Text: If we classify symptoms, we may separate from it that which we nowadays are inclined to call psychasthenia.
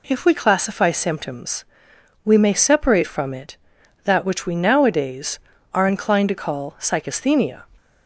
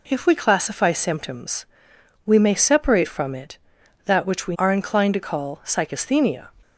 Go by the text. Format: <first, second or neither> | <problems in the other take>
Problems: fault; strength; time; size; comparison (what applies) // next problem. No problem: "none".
first | skips "nowadays"; at 4.5 s